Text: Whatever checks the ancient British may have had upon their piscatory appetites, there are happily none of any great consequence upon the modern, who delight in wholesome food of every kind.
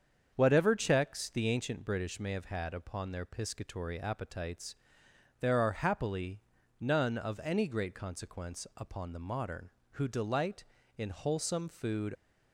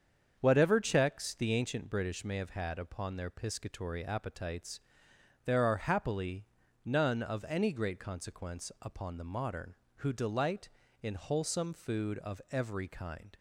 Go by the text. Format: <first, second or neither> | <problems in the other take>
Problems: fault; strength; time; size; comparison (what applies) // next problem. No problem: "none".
second | starts louder than the rest; until 1.3 s; 7 dB; strong in the second // pauses between "happily" and "none"; at 6.4 s; 0.40 s long; also in the second // stops before "of every kind"; at 12.1 s